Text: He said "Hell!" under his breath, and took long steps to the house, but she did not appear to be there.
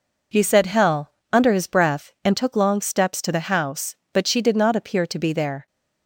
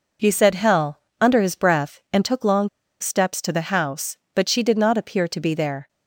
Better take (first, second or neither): first